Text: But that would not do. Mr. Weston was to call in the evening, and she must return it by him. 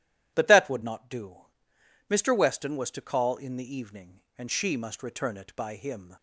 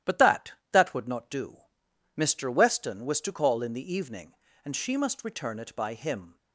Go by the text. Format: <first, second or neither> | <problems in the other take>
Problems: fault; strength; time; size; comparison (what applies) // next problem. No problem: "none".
first | starts louder than the rest; strong; until 1.2 s; 12 dB // says "that" twice; at 0.7 s